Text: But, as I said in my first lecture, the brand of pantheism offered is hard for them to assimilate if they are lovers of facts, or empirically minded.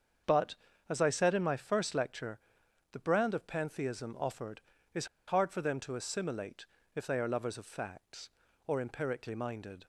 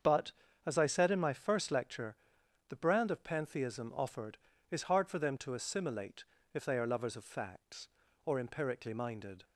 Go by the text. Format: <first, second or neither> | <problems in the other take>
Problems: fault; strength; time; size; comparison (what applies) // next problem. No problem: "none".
second | starts louder than the rest; until 1.5 s; 7 dB; also in the second // pauses between "is" and "hard"; slight; at 5.0 s; 0.21 s long // pauses between "assimilate" and "if"; slight; at 6.6 s; 0.30 s long; slight in the second